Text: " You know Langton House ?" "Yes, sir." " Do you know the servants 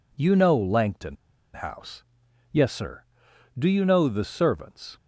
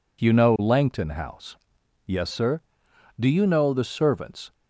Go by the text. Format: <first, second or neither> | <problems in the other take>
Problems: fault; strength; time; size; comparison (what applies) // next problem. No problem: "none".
second | pauses between "Langton" and "House"; at 1.1 s; 0.39 s long